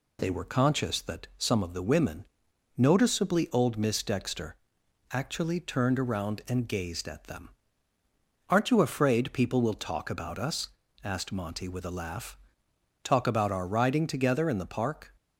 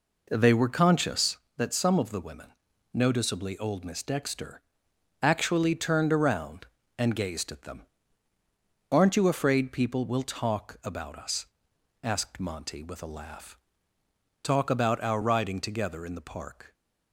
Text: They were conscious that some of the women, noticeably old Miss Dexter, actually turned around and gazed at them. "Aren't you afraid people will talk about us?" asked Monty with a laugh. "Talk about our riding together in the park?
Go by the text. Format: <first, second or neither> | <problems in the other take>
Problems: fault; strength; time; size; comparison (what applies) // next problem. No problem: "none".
first | starts louder than the rest; noticeable; until 1.5 s; 4 dB